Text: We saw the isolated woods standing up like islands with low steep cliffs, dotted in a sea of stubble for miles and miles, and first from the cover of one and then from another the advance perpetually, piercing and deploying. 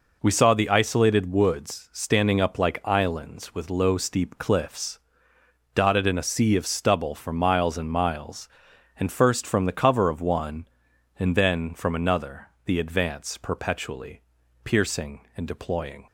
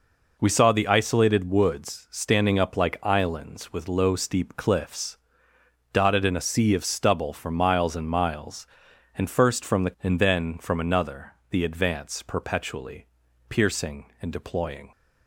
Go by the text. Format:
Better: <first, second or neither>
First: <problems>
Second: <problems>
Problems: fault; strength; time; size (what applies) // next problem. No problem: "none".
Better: first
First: pauses between "another" and "the"; slight; at 12.4 s; 0.16 s long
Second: skips "cover of one"; at 9.9 s // pauses between "another" and "the"; slight; at 11.3 s; 0.16 s long